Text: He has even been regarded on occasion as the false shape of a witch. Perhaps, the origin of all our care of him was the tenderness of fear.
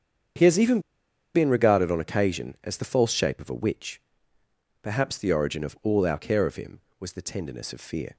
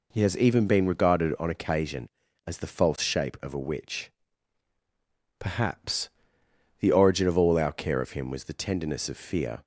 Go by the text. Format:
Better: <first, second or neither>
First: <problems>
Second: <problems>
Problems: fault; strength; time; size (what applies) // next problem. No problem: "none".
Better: second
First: starts louder than the rest; strong; until 1.9 s; 8 dB // pauses between "even" and "been"; noticeable; at 0.7 s; 0.55 s long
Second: none